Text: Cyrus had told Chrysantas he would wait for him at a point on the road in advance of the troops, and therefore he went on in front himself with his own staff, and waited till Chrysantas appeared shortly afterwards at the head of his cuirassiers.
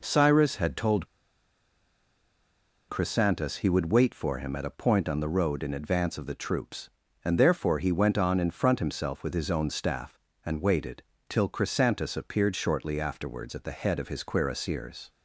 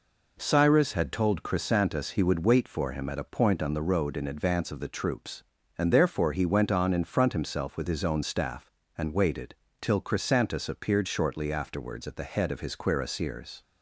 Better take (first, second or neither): second